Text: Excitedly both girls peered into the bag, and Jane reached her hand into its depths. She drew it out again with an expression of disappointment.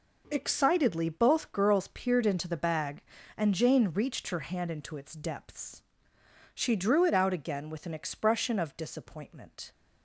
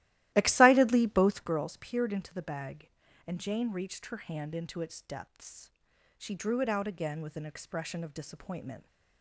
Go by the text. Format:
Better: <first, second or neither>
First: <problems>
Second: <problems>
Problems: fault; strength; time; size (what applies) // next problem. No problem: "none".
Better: first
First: none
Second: starts louder than the rest; strong; until 1.6 s; 15.5 dB